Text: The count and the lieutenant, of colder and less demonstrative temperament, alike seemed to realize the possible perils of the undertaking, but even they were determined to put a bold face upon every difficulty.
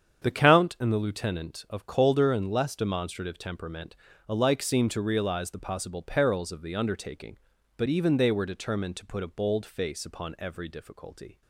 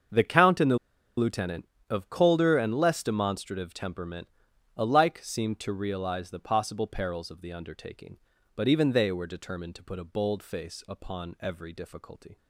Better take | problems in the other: first | starts louder than the rest; until 1.5 s; 7 dB; strong in the first // pauses between "the" and "lieutenant"; at 0.7 s; 0.40 s long

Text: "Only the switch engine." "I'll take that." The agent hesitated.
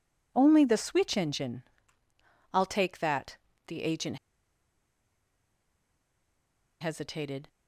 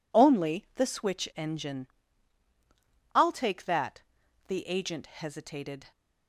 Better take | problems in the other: second | pauses between "agent" and "hesitated"; strong; at 4.1 s; 2.6 s long

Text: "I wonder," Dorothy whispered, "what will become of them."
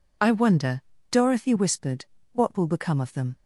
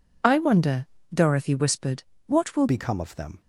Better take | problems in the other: first | changes voice at "become"; from 2.6 s on; 0.8 s long

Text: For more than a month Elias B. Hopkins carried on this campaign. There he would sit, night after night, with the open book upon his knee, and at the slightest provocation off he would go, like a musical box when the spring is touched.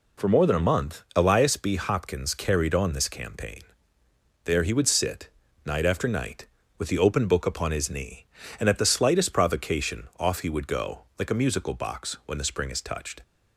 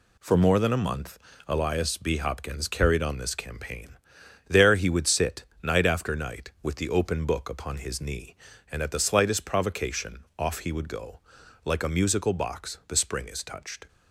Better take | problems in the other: first | pauses between "month" and "Elias"; slight; at 1.1 s; 0.30 s long // skips "when"; at 12.8 s

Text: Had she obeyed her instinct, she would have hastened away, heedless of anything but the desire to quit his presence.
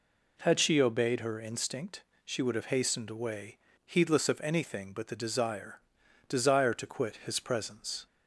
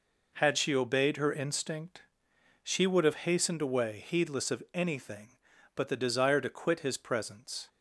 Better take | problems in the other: second | says "desire" twice; at 6.2 s

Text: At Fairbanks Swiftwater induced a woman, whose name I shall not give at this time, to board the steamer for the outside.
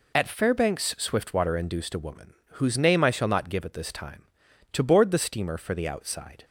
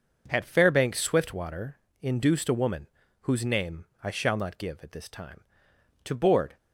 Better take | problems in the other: first | pauses between "Swiftwater" and "induced"; slight; at 1.7 s; 0.24 s long // pauses between "name" and "I"; slight; at 3.8 s; 0.18 s long // stops before "the steamer for the outside"; at 6.5 s

